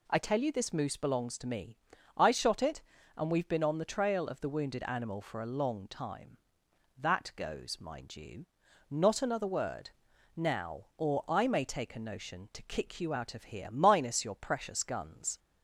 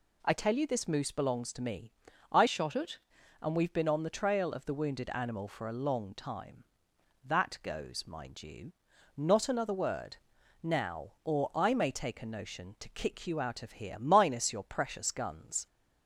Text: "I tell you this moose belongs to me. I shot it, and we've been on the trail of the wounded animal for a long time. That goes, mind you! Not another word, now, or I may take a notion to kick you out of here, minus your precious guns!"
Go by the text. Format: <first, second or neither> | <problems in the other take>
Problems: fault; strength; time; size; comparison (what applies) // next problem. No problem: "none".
first | changes voice from "shot" to "it"; from 2.4 to 2.9 s; 0.5 s long